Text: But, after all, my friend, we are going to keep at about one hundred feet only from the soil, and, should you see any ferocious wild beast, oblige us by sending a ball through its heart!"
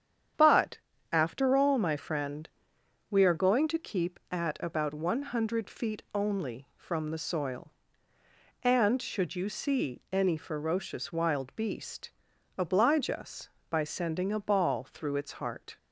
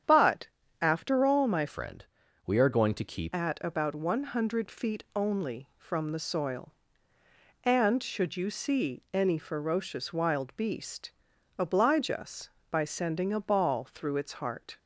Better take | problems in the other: first | starts louder than the rest; strong; until 1.4 s; 9 dB; strong in the first // changes voice from "friend" to "keep"; from 1.6 to 3.3 s; 1.7 s long

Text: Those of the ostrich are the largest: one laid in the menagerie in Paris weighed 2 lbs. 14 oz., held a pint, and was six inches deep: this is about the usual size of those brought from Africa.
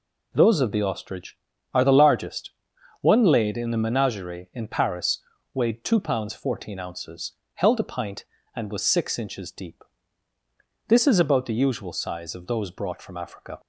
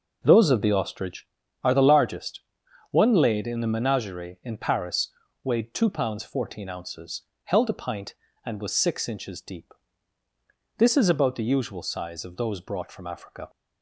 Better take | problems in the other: first | starts louder than the rest; noticeable; until 1.3 s; 6 dB // pauses between "Paris" and "weighed"; slight; at 5.1 s; 0.30 s long; slight in the first

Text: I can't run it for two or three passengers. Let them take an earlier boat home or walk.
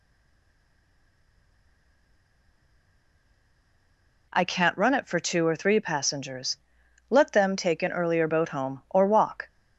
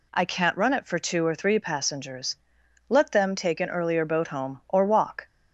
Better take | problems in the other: second | stays silent before the first word; strong; until 4.2 s; 4.2 s long

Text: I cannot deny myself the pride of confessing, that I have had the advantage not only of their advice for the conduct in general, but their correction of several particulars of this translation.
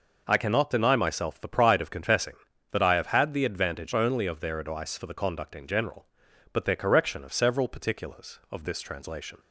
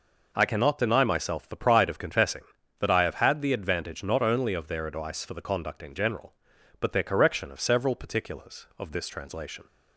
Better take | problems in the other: second | skips "not"; at 3.9 s

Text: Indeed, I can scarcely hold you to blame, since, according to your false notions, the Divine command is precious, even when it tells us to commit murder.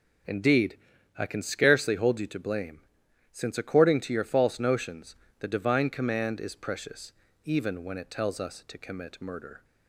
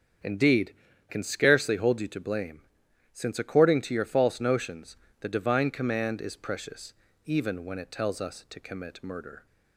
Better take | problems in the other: first | starts louder than the rest; strong; until 1.5 s; 7.5 dB // skips "I"; at 0.9 s

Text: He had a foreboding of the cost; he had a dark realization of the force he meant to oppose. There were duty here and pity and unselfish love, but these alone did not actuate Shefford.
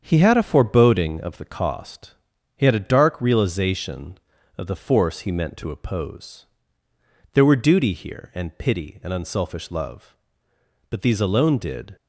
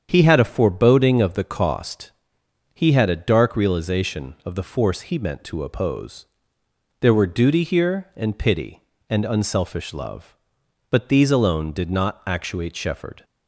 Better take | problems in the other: second | starts louder than the rest; strong; until 1.0 s; 7.5 dB; strong in the second // stops before "not actuate Shefford"; at 11.9 s

